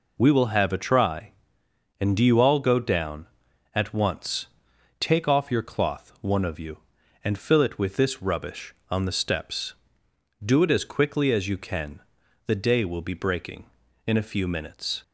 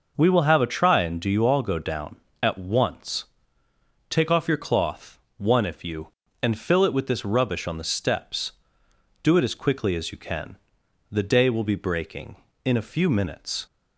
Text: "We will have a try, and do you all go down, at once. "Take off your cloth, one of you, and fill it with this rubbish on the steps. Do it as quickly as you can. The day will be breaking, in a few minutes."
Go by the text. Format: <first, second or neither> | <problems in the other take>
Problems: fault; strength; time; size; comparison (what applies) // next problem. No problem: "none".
first | says "if" for "of"; at 5.6 s